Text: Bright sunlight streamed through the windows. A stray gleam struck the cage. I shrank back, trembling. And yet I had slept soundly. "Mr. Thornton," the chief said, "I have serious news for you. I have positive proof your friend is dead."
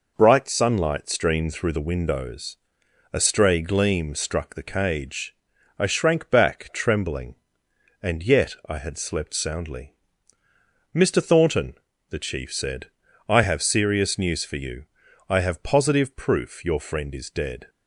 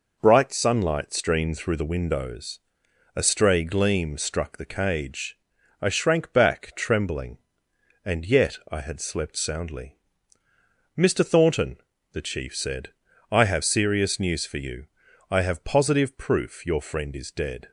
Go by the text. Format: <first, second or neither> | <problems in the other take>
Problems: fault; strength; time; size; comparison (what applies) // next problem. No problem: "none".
neither | pauses between "yet" and "I"; slight; the same in both